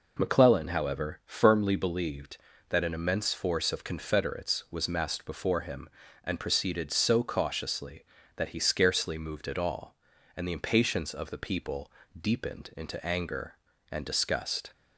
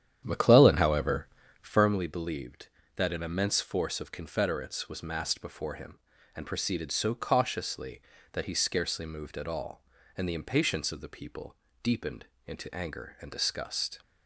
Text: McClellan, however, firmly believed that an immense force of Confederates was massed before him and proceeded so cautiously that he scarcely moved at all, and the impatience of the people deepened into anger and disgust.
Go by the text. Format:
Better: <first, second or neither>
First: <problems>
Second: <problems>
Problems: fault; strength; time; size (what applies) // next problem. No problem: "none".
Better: first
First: pauses between "people" and "deepened"; slight; at 11.9 s; 0.28 s long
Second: starts louder than the rest; strong; until 1.9 s; 9.5 dB // pauses between "people" and "deepened"; slight; at 11.5 s; 0.26 s long // pauses between "deepened" and "into"; slight; at 12.2 s; 0.22 s long